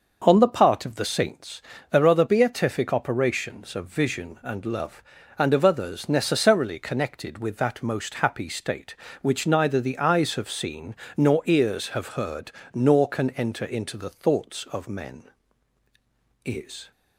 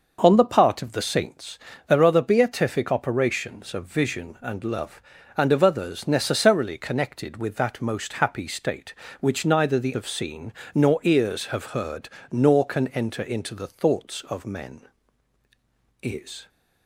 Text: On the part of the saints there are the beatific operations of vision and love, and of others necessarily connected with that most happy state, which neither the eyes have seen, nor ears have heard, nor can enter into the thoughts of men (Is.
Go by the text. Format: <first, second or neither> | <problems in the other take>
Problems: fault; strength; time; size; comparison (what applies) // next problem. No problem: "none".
first | starts louder than the rest; noticeable; until 1.2 s; 6 dB; noticeable in the first // pauses between "saints" and "there"; slight; at 1.5 s; 0.30 s long; slight in the first // skips "eyes"; at 9.9 s